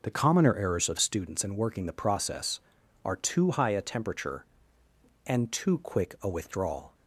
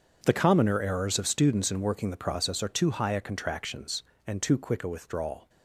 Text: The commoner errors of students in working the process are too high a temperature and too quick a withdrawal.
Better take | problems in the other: first | starts louder than the rest; until 1.2 s; 7 dB // says "contractions" for "temperature"; at 3.2 s

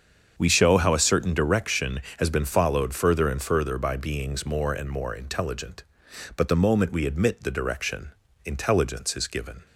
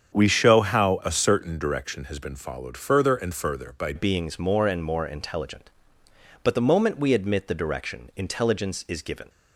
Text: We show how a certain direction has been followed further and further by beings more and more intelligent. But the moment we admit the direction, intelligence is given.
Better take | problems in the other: first | starts louder than the rest; strong; until 1.2 s; 7.5 dB; strong in the first // changes voice at "beings"; from 3.9 s on; 5.3 s long

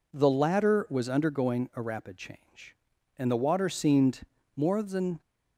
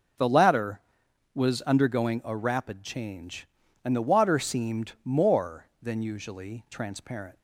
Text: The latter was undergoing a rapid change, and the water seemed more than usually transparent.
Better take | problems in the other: second | pauses between "seemed" and "more"; slight; at 4.2 s; 0.34 s long // stops before "usually transparent"; at 5.2 s

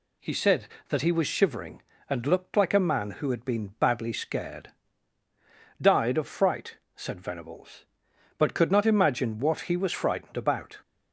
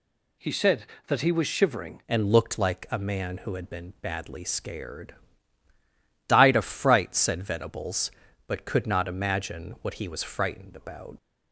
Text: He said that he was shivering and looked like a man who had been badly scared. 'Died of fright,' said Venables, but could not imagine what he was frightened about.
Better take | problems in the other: first | changes voice at "and"; from 2.0 s on; 9.1 s long

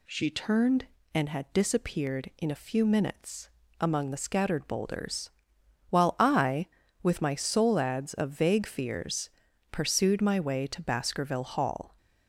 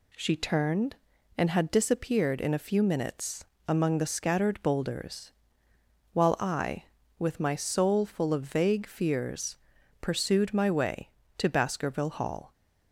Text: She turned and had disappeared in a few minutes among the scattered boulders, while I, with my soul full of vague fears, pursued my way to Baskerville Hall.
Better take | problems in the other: second | pauses between "minutes" and "among"; slight; at 3.4 s; 0.32 s long; slight in the second // says "ads" for "full"; at 7.7 s

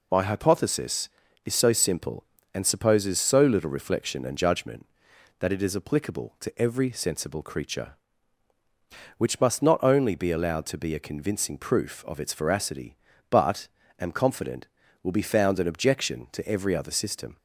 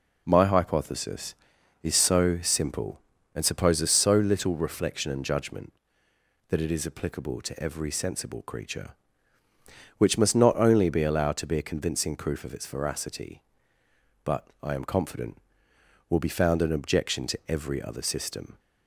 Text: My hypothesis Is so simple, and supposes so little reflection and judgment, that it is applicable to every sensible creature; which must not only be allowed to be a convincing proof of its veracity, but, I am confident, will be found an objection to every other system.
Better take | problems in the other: second | skips "I"; at 13.8 s

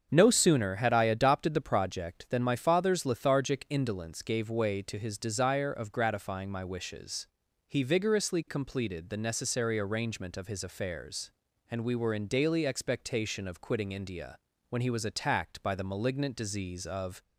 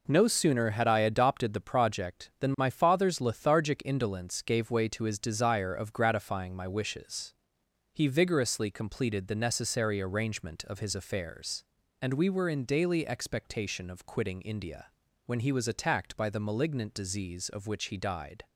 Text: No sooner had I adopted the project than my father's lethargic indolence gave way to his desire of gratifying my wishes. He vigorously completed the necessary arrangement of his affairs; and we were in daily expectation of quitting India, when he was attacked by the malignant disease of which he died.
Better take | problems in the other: second | starts louder than the rest; strong; until 1.1 s; 7 dB // stops before "which he died"; at 17.2 s

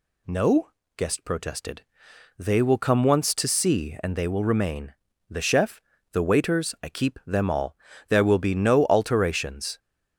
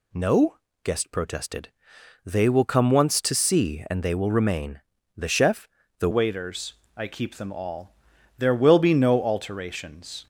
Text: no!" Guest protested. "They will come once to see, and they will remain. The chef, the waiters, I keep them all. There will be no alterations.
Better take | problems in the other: first | changes voice at "waiters"; from 6.1 s on; 4.1 s long

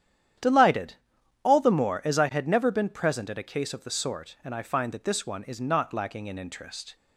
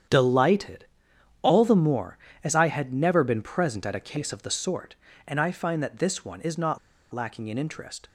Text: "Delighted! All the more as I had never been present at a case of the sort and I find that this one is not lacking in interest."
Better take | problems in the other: first | starts louder than the rest; strong; until 1.6 s; 9 dB; strong in the first // pauses between "not" and "lacking"; slight; at 6.7 s; 0.33 s long

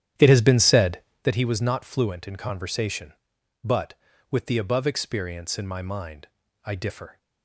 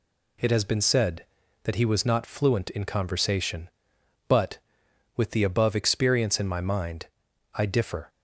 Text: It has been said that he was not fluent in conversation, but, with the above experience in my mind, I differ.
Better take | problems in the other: second | starts louder than the rest; strong; until 1.3 s; 10.5 dB

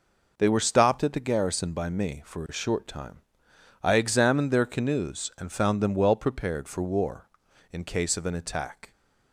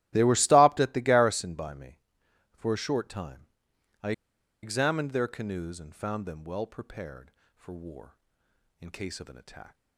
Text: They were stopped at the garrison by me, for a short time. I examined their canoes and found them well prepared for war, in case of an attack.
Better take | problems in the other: first | starts louder than the rest; strong; until 1.1 s; 14.5 dB // pauses between "I" and "examined"; noticeable; at 4.1 s; 0.51 s long

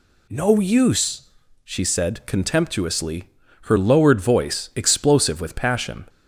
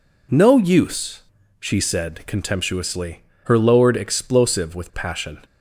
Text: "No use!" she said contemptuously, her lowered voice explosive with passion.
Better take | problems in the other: first | skips "voice"; at 3.9 s

